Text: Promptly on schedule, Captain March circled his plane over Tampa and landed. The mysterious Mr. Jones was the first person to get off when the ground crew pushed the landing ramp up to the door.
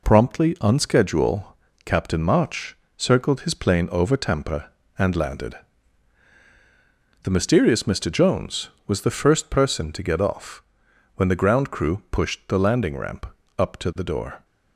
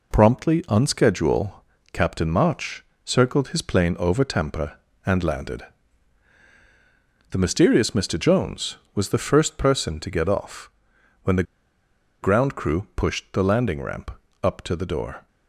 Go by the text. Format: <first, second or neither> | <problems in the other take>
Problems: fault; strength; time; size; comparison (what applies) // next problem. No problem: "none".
first | pauses between "March" and "circled"; slight; at 2.8 s; 0.22 s long; slight in the first // pauses between "off" and "when"; noticeable; at 10.6 s; 0.54 s long; noticeable in the first // pauses between "the" and "ground"; noticeable; at 11.4 s; 0.79 s long // pauses between "ramp" and "up"; slight; at 14.0 s; 0.34 s long; slight in the first